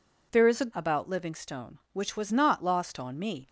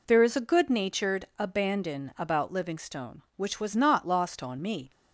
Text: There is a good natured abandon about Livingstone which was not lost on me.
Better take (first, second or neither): second